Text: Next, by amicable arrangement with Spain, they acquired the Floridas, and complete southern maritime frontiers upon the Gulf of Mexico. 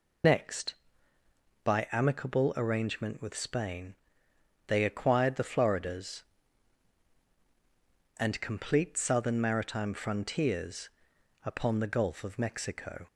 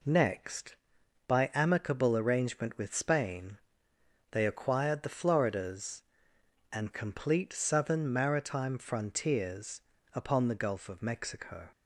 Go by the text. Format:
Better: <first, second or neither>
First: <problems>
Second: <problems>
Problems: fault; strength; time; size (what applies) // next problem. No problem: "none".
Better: second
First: loses the start of "Next"; at 0.2 s; 45 ms // pauses between "frontiers" and "upon"; noticeable; at 10.9 s; 0.52 s long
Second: pauses between "frontiers" and "upon"; slight; at 9.8 s; 0.32 s long